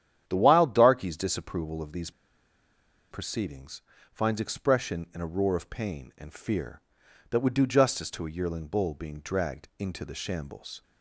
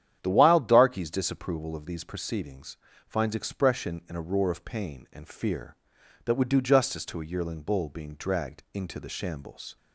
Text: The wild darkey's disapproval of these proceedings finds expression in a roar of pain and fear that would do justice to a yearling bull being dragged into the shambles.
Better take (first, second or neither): second